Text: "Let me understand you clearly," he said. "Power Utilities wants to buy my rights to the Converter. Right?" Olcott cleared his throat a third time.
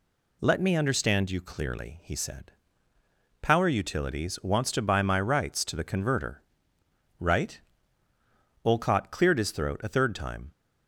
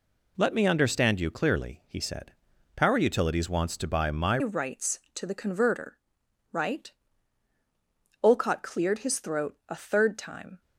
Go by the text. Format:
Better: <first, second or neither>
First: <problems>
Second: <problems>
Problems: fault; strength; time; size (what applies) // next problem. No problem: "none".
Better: first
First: none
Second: changes voice at "rights"; from 4.4 s on; 6.2 s long